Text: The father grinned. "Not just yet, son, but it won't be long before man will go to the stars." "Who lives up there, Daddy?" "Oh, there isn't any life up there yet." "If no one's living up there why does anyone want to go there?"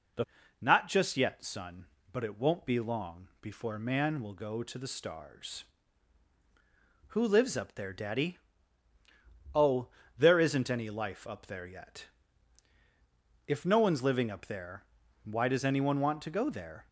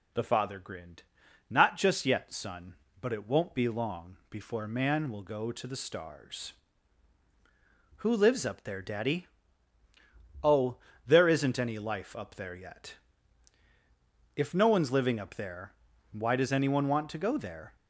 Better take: second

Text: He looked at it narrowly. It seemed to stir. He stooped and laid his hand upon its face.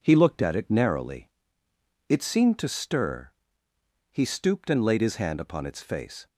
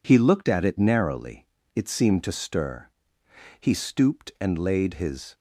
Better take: first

